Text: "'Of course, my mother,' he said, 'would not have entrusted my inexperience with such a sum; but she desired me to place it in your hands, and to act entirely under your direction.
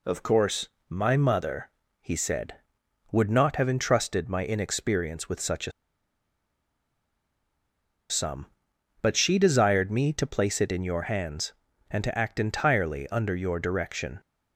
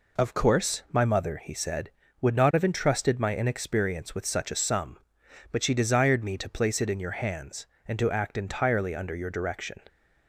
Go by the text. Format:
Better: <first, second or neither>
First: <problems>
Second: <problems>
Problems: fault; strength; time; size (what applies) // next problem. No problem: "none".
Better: second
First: pauses between "a" and "sum"; strong; at 5.7 s; 2.3 s long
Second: none